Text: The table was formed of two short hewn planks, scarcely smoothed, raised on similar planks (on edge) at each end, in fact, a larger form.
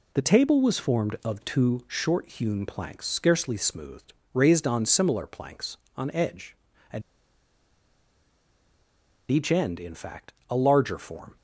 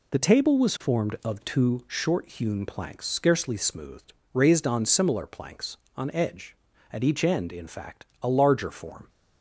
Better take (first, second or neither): second